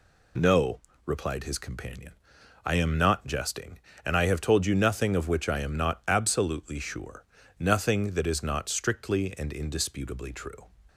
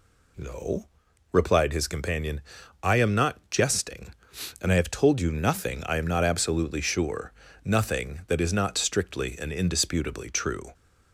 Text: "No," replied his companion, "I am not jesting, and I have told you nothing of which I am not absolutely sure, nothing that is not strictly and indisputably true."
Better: first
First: none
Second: skips "of which"; at 5.8 s

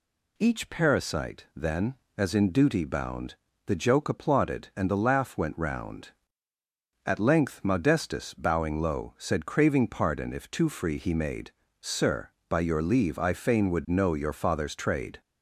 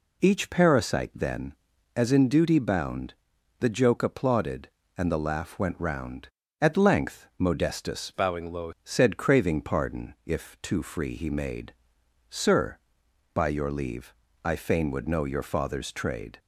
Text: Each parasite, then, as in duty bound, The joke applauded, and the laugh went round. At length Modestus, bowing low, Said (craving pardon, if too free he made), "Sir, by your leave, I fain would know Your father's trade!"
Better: first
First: none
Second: changes voice from "bowing" to "low"; from 8.1 to 8.7 s; 0.6 s long

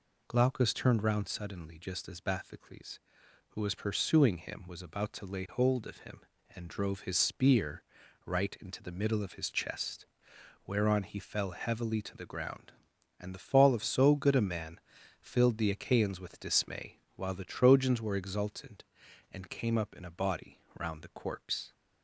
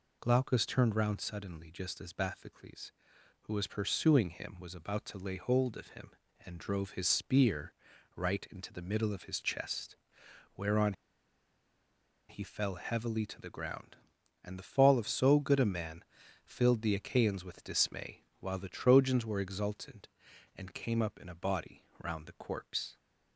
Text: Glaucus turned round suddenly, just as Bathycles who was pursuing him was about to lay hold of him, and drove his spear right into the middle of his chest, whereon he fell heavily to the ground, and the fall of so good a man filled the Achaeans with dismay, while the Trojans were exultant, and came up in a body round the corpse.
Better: first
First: pauses between "spear" and "right"; at 7.8 s; 0.42 s long // pauses between "man" and "filled"; at 14.7 s; 0.40 s long // pauses between "body" and "round"; slight; at 20.6 s; 0.18 s long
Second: pauses between "spear" and "right"; at 7.7 s; 0.42 s long // pauses between "whereon" and "he"; strong; at 10.9 s; 1.3 s long // pauses between "man" and "filled"; at 16.0 s; 0.40 s long // pauses between "body" and "round"; slight; at 21.8 s; 0.18 s long

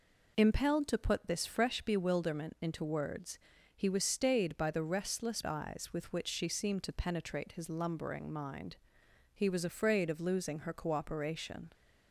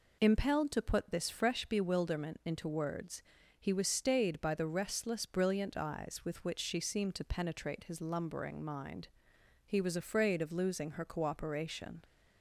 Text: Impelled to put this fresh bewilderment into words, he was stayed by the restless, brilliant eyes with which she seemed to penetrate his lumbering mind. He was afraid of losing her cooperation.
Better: second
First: skips "brilliant"; at 5.4 s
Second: none

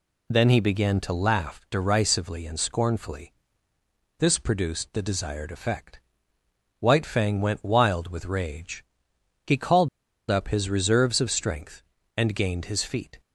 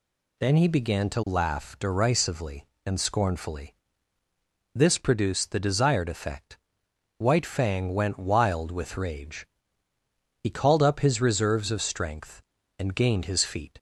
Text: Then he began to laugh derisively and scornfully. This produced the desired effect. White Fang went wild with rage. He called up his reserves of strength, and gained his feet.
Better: second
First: pauses between "called" and "up"; at 9.8 s; 0.42 s long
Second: none

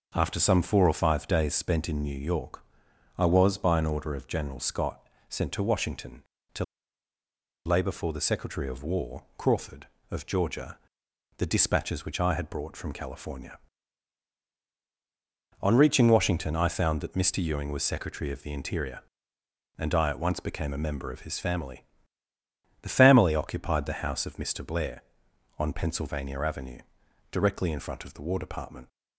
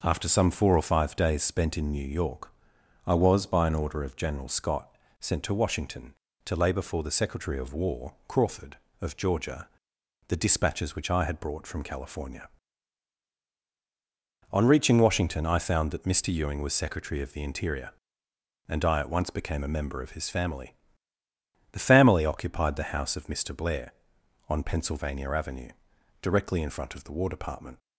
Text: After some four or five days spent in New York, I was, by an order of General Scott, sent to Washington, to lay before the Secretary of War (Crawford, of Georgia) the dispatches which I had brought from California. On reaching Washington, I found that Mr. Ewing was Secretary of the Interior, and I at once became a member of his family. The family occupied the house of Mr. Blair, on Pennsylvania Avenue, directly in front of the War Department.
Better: second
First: pauses between "to" and "lay"; at 6.6 s; 1.0 s long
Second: none

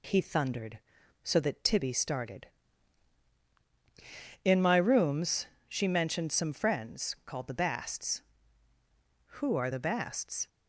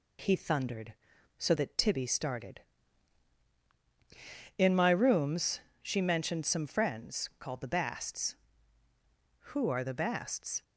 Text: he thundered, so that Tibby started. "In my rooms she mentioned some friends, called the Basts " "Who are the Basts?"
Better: neither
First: pauses between "rooms" and "she"; slight; at 5.4 s; 0.20 s long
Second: pauses between "rooms" and "she"; slight; at 5.6 s; 0.20 s long

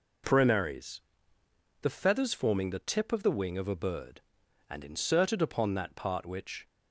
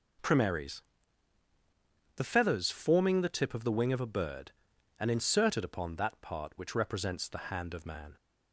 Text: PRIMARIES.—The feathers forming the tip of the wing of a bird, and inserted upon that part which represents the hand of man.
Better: second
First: stops before "represents the hand of man"; at 6.6 s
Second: none

